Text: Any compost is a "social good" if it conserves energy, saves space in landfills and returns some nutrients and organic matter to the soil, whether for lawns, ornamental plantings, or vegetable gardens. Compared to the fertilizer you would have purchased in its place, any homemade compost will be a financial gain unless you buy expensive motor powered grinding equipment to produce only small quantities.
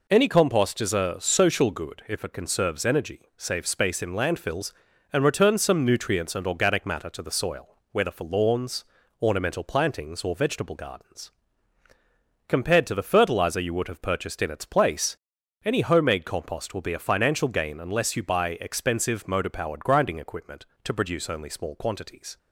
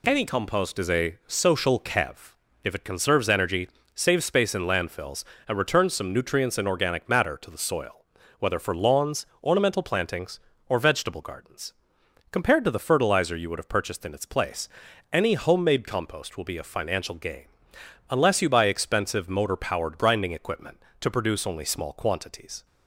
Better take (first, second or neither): first